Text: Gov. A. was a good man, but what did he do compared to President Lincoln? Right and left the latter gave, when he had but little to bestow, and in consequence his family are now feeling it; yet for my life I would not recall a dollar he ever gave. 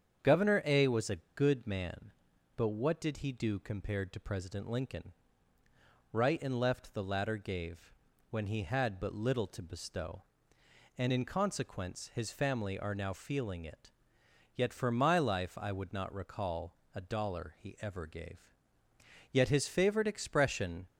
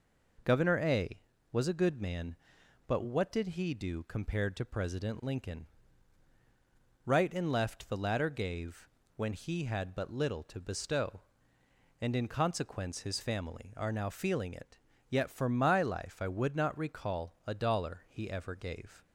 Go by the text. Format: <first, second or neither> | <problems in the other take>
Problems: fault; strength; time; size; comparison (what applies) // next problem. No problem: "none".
second | starts louder than the rest; strong; until 1.4 s; 8 dB // pauses between "a" and "good"; slight; at 1.1 s; 0.16 s long // pauses between "recall" and "a"; slight; at 16.7 s; 0.22 s long // goes on to say "Yet his favorite expression"; from 19.3 s on; 1.5 s long